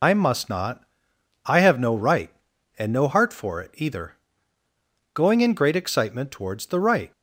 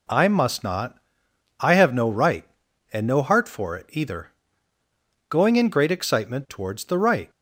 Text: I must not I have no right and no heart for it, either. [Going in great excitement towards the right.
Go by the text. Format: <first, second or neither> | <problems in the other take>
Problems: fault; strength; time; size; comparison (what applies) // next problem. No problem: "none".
second | loses the start of "I"; at 0.0 s; 75 ms // pauses between "not" and "I"; noticeable; at 0.8 s; 0.62 s long; noticeable in the second